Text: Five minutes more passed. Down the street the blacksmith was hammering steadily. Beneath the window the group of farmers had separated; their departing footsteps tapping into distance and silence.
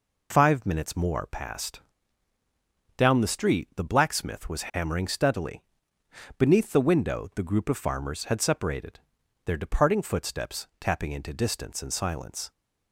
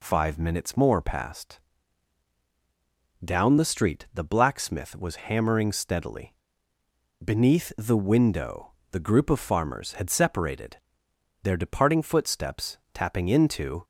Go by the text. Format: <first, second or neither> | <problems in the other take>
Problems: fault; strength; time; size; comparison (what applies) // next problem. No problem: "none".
first | pauses between "window" and "the"; slight; at 8.7 s; 0.22 s long // pauses between "footsteps" and "tapping"; slight; at 12.7 s; 0.16 s long // stops before "distance and silence"; at 13.8 s